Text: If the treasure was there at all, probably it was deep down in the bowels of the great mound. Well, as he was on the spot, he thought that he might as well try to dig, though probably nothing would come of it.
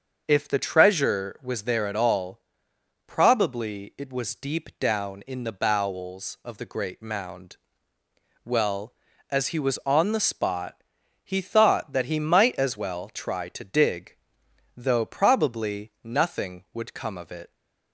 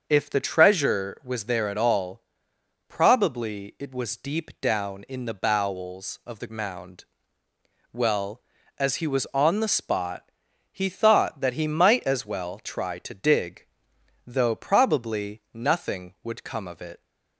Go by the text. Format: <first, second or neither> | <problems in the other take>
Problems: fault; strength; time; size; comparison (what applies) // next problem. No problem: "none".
first | starts louder than the rest; until 1.0 s; 6.5 dB; also in the first // skips "great"; at 6.4 s